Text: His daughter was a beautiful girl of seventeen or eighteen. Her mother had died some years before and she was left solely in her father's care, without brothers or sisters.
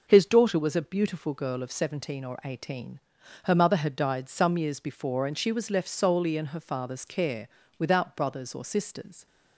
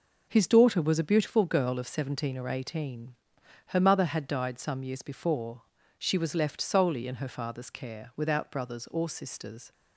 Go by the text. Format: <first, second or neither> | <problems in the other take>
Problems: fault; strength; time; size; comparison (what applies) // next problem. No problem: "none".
first | skips "and"; at 5.7 s